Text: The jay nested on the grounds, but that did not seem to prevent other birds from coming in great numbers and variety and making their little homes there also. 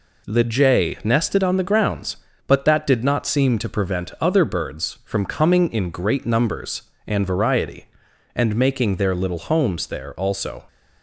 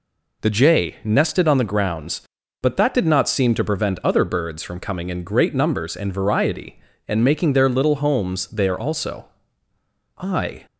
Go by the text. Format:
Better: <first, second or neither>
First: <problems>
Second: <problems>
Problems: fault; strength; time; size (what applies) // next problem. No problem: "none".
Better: first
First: none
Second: goes on to say "I"; slight; from 10.1 s on; 0.48 s long